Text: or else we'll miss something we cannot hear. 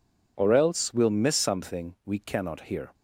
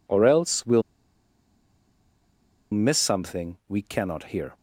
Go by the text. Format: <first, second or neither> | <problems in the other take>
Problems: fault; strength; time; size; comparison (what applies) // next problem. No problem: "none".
first | pauses between "we'll" and "miss"; strong; at 0.8 s; 1.9 s long